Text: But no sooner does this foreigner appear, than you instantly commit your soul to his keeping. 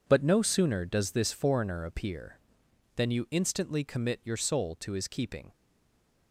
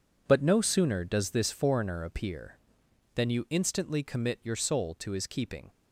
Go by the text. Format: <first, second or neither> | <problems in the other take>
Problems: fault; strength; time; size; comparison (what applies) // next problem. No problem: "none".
second | stays silent after the last word; slight; from 5.5 s on; 0.8 s long